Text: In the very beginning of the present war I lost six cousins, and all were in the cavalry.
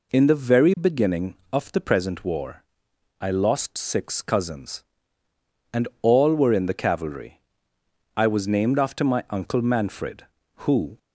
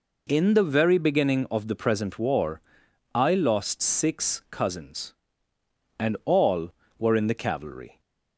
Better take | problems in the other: second | pauses between "war" and "I"; noticeable; at 2.6 s; 0.58 s long; noticeable in the second // goes on to say "I was named after my uncle Manfred who"; strong; from 8.1 s on; 2.8 s long

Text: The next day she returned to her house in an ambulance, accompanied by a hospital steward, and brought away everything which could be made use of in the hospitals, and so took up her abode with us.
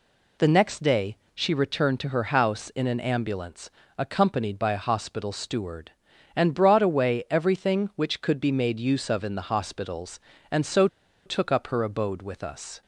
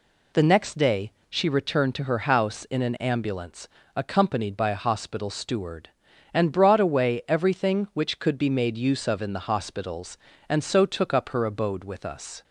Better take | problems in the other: second | pauses between "day" and "she"; slight; at 1.1 s; 0.20 s long; slight in the second // pauses between "so" and "took"; at 10.8 s; 0.38 s long

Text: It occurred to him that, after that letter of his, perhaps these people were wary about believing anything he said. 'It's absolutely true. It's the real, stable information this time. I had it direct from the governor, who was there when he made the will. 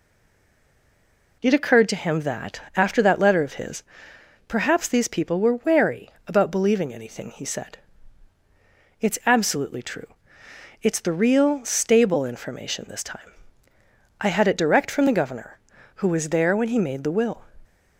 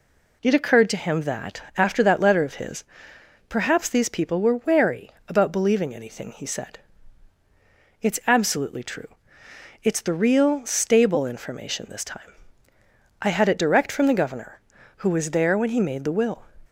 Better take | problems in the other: second | stays silent before the first word; noticeable; until 1.4 s; 1.4 s long // pauses between "wary" and "about"; slight; at 6.0 s; 0.18 s long; slight in the second

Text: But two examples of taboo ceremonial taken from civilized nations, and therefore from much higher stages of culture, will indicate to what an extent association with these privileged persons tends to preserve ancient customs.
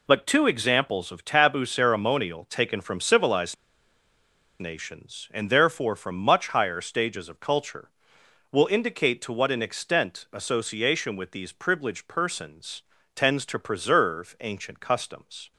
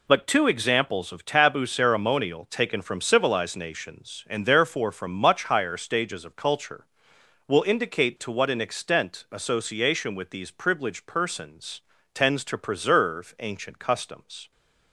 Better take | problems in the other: second | pauses between "civilized" and "nations"; at 3.5 s; 1.0 s long // pauses between "persons" and "tends"; slight; at 12.8 s; 0.34 s long; slight in the second

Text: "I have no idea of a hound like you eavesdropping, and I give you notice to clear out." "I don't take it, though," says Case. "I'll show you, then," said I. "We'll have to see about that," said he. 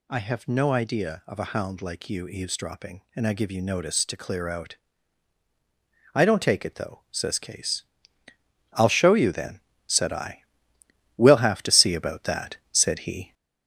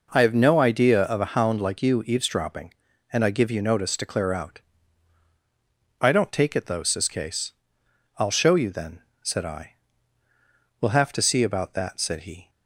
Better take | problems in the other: second | gets louder; noticeable; throughout; 4 dB

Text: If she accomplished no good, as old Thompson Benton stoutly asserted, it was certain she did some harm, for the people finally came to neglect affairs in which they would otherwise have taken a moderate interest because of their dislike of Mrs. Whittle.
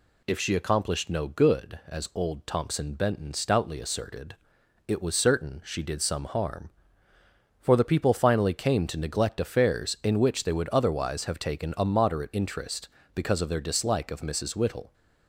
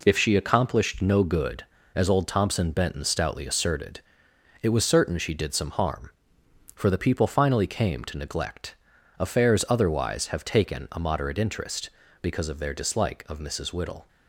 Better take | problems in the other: first | pauses between "neglect" and "affairs"; noticeable; at 8.7 s; 0.46 s long // skips "in which they would"; at 9.6 s

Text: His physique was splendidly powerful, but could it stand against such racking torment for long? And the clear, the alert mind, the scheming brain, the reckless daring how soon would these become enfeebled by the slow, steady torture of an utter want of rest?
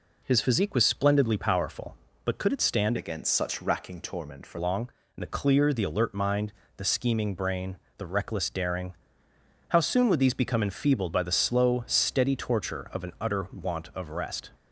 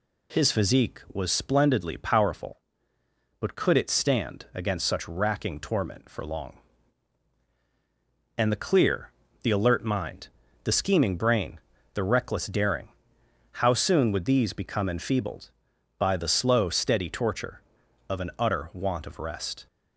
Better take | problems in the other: second | changes voice from "against" to "for"; from 2.9 to 4.5 s; 1.6 s long // pauses between "daring" and "how"; noticeable; at 8.9 s; 0.76 s long; noticeable in the second

